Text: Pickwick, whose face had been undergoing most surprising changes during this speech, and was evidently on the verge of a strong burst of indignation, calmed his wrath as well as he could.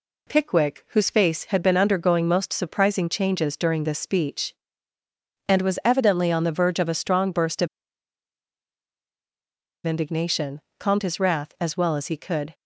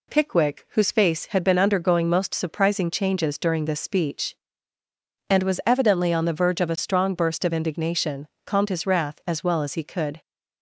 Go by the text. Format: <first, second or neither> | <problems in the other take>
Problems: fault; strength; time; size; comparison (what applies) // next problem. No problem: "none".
second | pauses between "of" and "indignation"; strong; at 7.6 s; 2.1 s long